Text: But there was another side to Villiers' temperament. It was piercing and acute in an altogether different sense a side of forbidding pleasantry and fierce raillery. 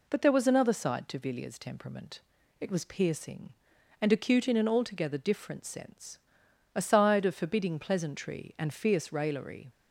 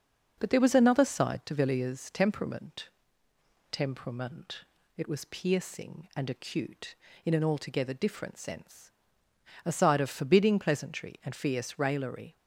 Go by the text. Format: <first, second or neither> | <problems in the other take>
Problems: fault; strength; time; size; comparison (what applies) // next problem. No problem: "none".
first | says "temperament" twice; at 3.6 s // pauses between "sense" and "a"; noticeable; at 8.9 s; 0.74 s long; noticeable in the first